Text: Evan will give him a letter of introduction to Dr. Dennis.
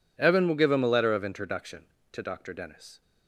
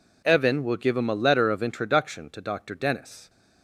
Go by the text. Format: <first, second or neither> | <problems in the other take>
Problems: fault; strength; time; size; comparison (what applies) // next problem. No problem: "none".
neither | none